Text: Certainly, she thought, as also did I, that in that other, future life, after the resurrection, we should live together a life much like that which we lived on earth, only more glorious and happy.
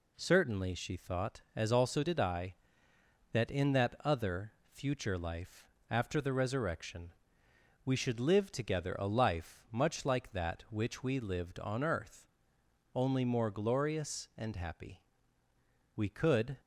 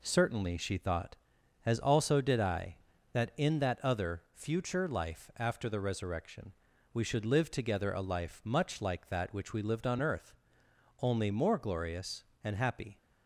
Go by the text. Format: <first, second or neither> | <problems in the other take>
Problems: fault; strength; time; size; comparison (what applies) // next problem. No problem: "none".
second | goes on to say "We could"; noticeable; from 15.9 s on; 0.62 s long